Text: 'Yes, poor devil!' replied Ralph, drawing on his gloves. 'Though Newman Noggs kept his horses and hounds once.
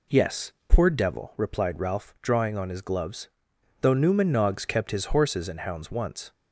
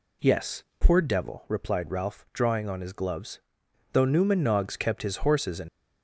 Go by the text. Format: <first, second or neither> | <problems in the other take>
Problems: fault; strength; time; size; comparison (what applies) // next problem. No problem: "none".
first | stops before "hounds once"; at 5.6 s